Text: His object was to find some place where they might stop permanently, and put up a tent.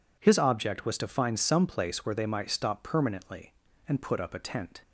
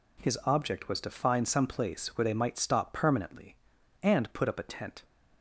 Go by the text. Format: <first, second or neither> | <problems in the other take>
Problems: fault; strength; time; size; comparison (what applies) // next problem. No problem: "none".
neither | none